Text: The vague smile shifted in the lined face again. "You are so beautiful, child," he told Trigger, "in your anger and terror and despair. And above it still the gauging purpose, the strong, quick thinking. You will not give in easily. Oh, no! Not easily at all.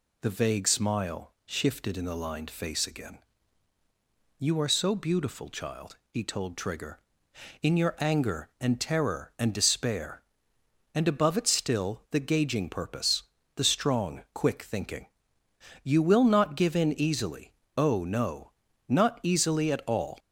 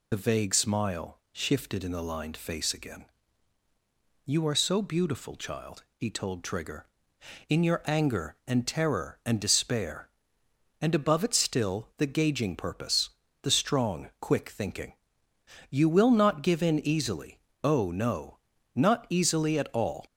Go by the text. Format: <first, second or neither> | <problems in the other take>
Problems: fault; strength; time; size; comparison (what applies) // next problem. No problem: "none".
first | loses the start of "The"; at 0.1 s; 25 ms